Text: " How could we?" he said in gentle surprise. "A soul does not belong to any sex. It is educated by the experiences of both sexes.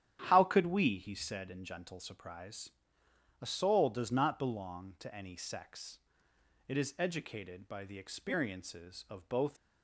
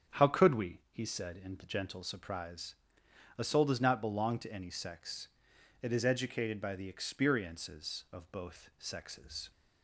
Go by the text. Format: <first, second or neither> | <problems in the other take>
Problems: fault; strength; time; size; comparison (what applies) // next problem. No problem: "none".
second | starts louder than the rest; strong; until 1.2 s; 10.5 dB; strong in the second // stops before "sexes"; at 9.5 s